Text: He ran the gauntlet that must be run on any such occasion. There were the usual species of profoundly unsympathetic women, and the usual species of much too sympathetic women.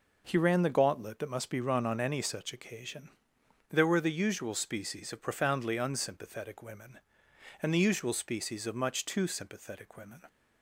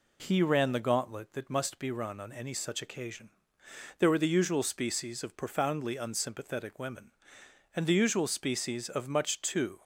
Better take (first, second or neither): first